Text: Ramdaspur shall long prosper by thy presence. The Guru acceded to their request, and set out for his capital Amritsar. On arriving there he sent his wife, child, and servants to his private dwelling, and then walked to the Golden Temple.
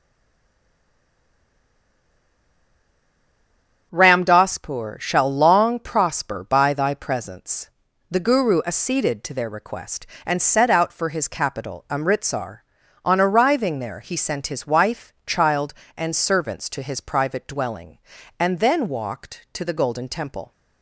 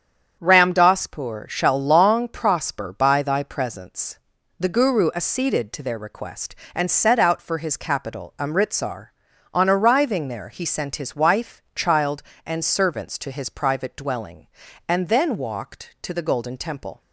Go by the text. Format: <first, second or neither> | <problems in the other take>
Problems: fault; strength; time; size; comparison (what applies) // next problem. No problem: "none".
second | stays silent before the first word; strong; until 3.9 s; 3.9 s long // starts louder than the rest; strong; until 4.9 s; 8 dB; strong in the second